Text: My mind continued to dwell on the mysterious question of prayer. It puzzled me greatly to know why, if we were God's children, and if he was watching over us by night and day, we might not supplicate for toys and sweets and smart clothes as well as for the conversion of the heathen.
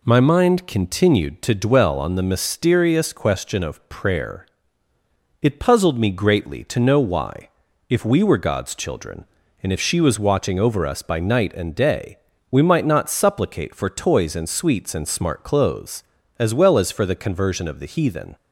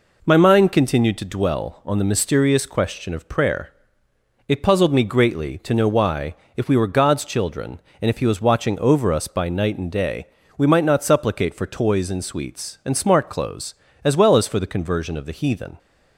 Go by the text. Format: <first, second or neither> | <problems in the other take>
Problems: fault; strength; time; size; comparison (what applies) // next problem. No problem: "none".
second | says "she" for "he"; at 9.8 s